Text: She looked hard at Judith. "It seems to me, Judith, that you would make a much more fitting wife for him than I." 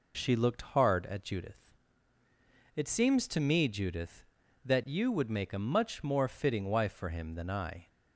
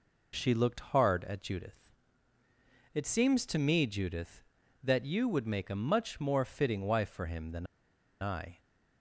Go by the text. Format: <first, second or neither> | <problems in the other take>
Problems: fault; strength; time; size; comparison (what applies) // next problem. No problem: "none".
first | pauses between "than" and "I"; noticeable; at 7.6 s; 0.56 s long